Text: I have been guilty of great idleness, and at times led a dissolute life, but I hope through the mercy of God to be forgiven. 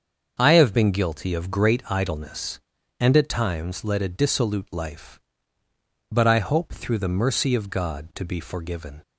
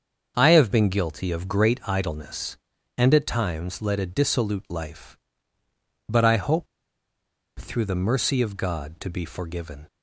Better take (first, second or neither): first